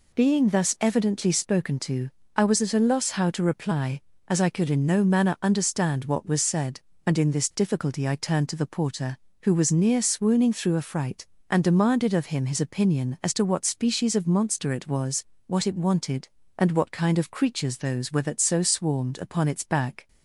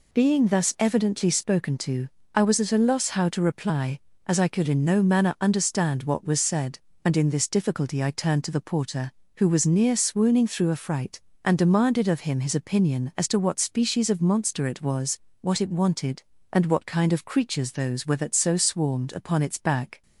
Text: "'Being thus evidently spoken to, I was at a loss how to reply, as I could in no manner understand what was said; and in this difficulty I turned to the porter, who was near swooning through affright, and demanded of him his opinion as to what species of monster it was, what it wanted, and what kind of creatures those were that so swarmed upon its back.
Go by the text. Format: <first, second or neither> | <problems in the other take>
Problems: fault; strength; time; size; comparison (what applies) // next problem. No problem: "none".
neither | none